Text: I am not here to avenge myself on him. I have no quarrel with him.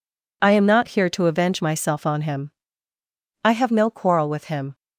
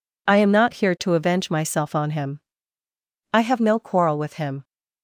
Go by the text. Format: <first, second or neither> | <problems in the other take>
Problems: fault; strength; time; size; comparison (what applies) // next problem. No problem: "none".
neither | none